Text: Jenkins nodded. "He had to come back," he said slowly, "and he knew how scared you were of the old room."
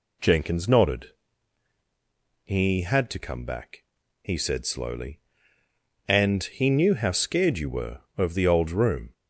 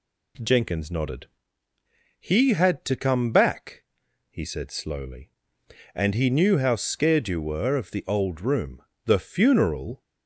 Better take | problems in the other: first | goes on to say "The funeral"; noticeable; from 9.0 s on; 0.96 s long

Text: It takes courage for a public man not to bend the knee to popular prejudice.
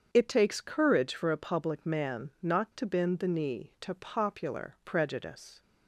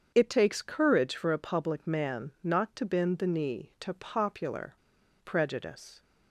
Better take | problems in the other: first | starts louder than the rest; strong; until 1.1 s; 7 dB; strong in the first // pauses between "popular" and "prejudice"; noticeable; at 4.7 s; 0.48 s long

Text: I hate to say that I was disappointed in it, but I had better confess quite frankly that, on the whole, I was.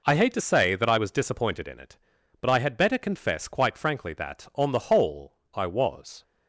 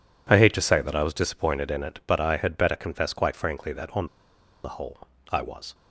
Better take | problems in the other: first | pauses between "on" and "the"; noticeable; at 4.0 s; 0.58 s long

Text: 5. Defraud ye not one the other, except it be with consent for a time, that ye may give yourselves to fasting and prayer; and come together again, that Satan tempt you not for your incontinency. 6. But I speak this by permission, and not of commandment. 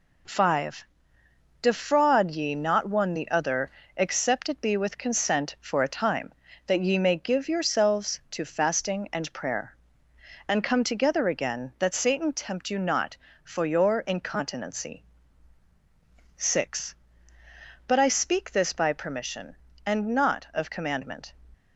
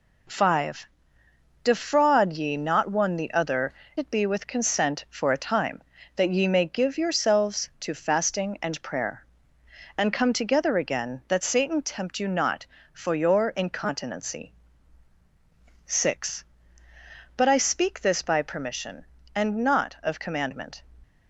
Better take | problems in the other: first | skips "except"; at 3.8 s

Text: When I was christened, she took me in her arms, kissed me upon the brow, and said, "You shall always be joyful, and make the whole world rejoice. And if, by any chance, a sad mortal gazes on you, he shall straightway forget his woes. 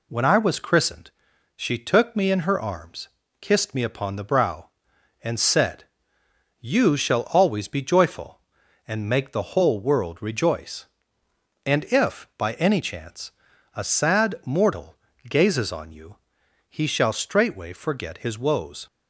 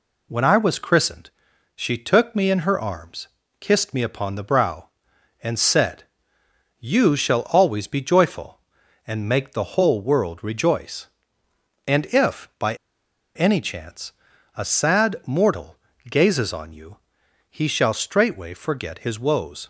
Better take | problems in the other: first | pauses between "by" and "any"; noticeable; at 12.7 s; 0.60 s long // pauses between "mortal" and "gazes"; slight; at 15.7 s; 0.34 s long; slight in the first

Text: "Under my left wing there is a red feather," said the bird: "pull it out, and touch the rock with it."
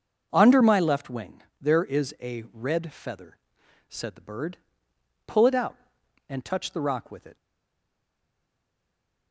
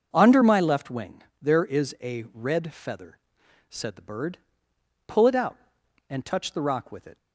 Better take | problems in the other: second | pauses between "wing" and "there"; slight; at 1.4 s; 0.18 s long; slight in the second // stays silent after the last word; noticeable; from 7.3 s on; 2.0 s long

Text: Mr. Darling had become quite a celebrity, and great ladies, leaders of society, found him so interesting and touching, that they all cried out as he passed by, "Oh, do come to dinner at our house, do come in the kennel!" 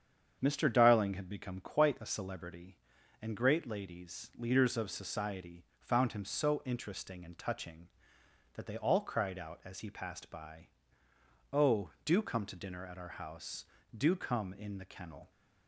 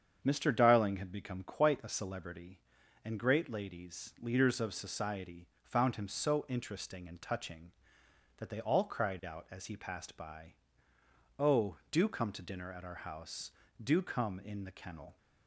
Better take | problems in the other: neither | starts louder than the rest; strong; the same in both

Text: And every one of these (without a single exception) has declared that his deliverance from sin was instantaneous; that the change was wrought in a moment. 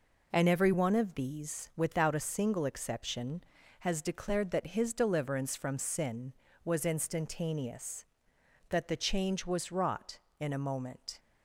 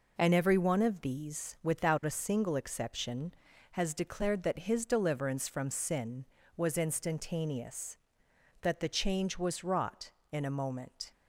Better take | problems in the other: neither | none

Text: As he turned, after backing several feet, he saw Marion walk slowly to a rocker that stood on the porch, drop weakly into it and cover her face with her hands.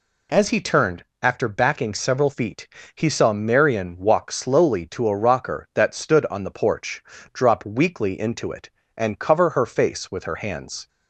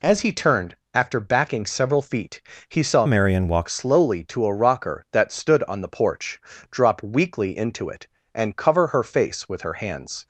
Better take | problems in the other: first | changes voice from "Marion" to "walk"; from 3.0 to 3.6 s; 0.6 s long

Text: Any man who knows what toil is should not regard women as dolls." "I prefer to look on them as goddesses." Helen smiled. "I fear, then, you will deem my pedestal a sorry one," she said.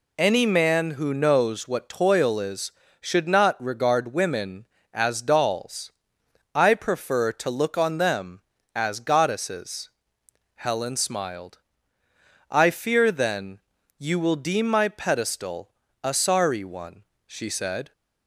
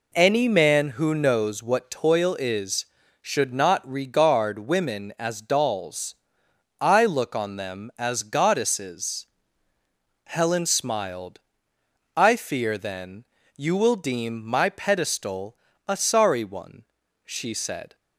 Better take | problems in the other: first | skips "prefer to"; at 7.0 s // pauses between "pedestal" and "a"; slight; at 15.5 s; 0.32 s long; slight in the first

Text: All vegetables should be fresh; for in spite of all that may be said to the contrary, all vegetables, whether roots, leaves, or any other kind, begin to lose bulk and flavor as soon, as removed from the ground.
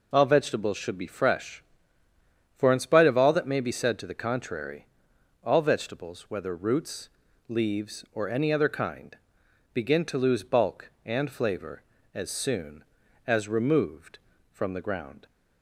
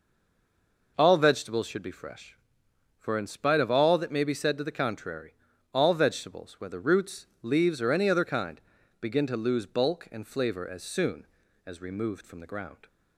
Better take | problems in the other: first | stays silent before the first word; slight; until 0.9 s; 0.9 s long

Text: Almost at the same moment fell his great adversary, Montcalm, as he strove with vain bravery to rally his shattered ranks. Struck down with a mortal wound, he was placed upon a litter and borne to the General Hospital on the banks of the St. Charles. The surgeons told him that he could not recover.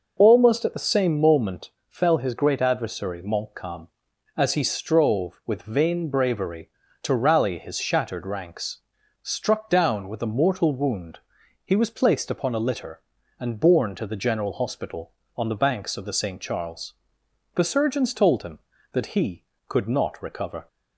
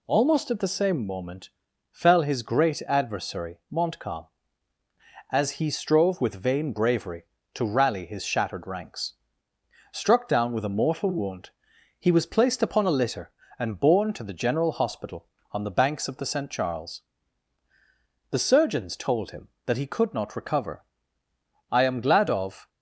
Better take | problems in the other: first | pauses between "moment" and "fell"; at 1.4 s; 0.42 s long; slight in the first // goes on to say "I am glad of"; noticeable; from 21.7 s on; 0.98 s long

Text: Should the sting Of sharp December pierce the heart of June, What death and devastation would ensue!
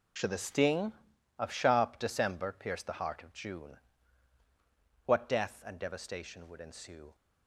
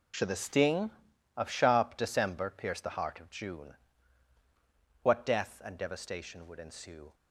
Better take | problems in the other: neither | none

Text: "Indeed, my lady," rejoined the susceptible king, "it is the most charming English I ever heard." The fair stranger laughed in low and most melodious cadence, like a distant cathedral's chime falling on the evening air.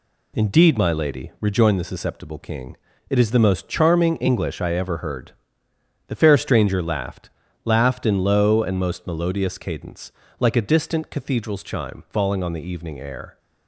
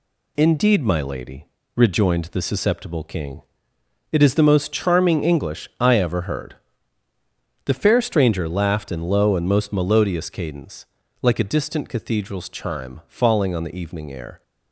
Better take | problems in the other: second | says "laughed" twice; at 7.6 s

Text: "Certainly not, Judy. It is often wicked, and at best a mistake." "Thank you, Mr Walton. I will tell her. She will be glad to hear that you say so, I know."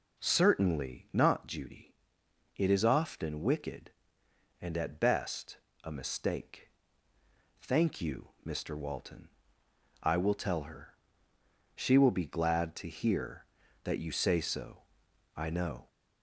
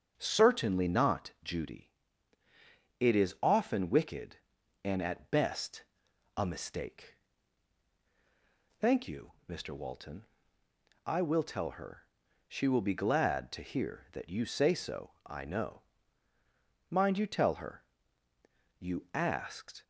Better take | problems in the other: first | starts louder than the rest; until 1.1 s; 6.5 dB // pauses between "best" and "a"; noticeable; at 5.8 s; 0.54 s long; slight in the first // goes on to say "Mind you tell her you asked"; strong; from 16.8 s on; 2.9 s long

